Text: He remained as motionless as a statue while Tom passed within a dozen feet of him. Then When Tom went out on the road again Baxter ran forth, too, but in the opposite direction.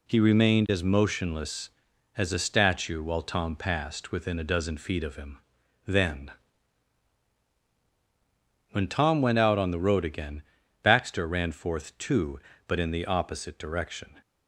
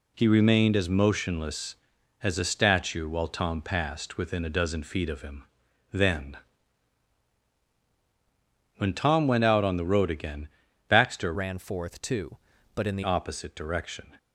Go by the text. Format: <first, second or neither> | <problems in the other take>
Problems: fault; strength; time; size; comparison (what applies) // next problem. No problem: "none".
first | pauses between "Then" and "When"; strong; at 6.3 s; 2.4 s long; strong in the first // pauses between "again" and "Baxter"; at 10.4 s; 0.40 s long; also in the first // changes voice from "ran" to "the"; from 11.3 to 13.0 s; 1.7 s long